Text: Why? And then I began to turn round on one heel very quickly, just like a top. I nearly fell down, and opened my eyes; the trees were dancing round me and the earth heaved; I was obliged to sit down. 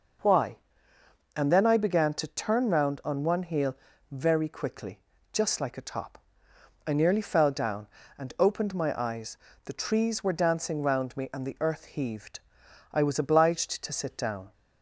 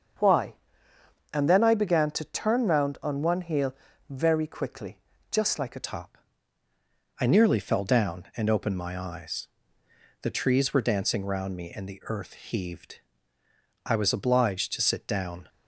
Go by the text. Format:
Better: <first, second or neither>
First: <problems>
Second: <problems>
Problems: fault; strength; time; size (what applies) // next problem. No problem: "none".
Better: first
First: pauses between "heel" and "very"; slight; at 3.7 s; 0.34 s long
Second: starts louder than the rest; until 1.9 s; 7 dB // pauses between "heel" and "very"; slight; at 3.7 s; 0.34 s long // changes voice at "top"; from 5.8 s on; 9.6 s long